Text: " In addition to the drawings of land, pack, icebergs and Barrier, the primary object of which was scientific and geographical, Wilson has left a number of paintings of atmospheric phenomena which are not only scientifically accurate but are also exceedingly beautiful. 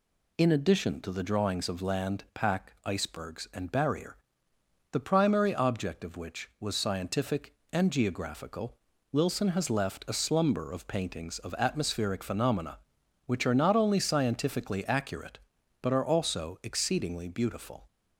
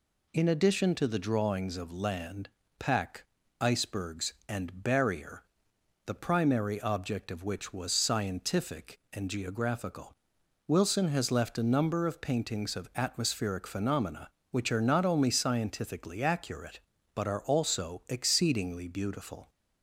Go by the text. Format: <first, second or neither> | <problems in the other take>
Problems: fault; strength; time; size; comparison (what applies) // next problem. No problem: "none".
second | says "slumber" for "number"; at 10.1 s